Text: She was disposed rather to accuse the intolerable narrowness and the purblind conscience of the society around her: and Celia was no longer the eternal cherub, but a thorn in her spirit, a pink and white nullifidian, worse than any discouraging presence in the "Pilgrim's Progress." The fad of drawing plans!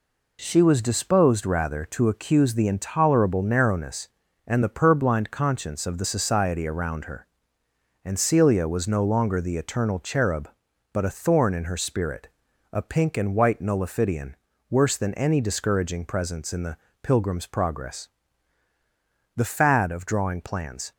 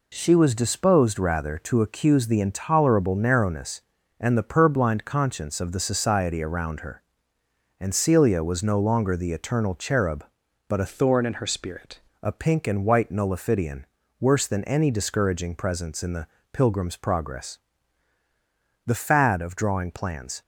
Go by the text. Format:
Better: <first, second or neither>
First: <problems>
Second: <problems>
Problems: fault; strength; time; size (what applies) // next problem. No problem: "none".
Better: first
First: pauses between "the" and "Pilgrim's"; slight; at 16.7 s; 0.24 s long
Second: changes voice from "thorn" to "spirit"; from 10.8 to 11.9 s; 1.1 s long // pauses between "the" and "Pilgrim's"; slight; at 16.2 s; 0.24 s long